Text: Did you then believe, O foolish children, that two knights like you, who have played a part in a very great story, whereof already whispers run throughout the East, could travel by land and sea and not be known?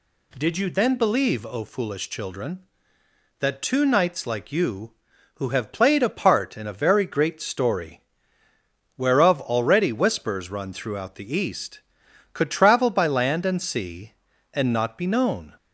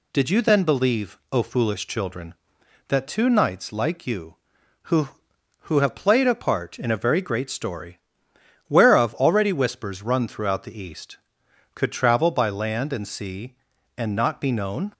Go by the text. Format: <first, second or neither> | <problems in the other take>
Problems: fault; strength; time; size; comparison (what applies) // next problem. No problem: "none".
first | says "who" twice; at 5.6 s